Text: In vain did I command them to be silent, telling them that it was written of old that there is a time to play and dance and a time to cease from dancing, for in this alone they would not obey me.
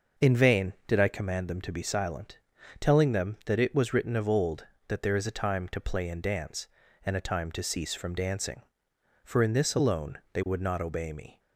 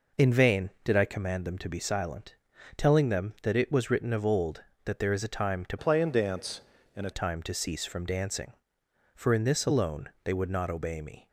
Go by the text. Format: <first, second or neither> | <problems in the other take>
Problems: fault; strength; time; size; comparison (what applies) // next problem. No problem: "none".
first | changes voice from "play" to "a"; from 5.7 to 7.0 s; 1.3 s long // pauses between "alone" and "they"; slight; at 10.0 s; 0.16 s long; slight in the first